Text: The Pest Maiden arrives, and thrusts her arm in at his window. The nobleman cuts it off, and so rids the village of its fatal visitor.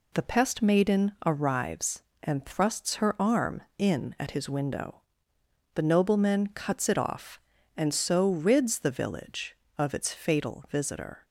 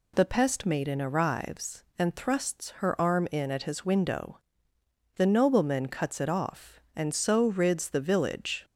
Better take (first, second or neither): first